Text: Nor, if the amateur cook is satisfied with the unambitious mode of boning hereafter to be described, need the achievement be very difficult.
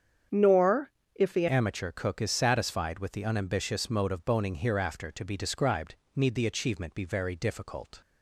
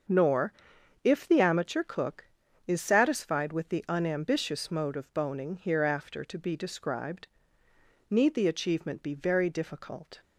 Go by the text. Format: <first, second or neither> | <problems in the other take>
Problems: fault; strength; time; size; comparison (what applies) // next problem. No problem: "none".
second | starts louder than the rest; strong; until 1.5 s; 7.5 dB; also in the second // changes voice at "amateur"; from 1.4 s on; 6.6 s long